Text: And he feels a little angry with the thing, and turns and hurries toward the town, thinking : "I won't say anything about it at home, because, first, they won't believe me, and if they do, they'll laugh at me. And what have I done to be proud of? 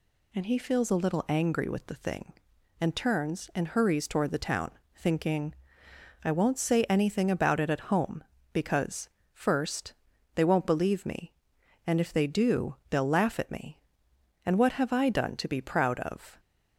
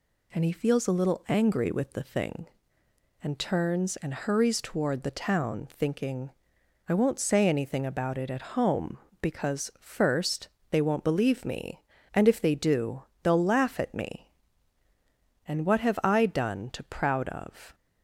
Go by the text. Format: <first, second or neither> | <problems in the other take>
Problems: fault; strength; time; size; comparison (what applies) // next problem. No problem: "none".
first | skips "be"; at 16.8 s